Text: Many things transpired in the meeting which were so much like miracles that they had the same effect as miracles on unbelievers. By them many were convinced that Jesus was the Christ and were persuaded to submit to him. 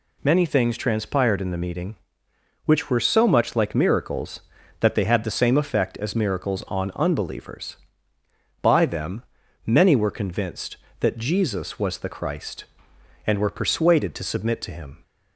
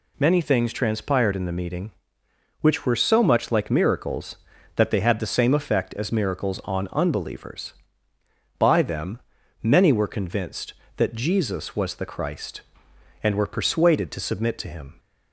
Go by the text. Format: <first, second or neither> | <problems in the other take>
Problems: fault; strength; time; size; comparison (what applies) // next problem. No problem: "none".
neither | pauses between "them" and "many"; the same in both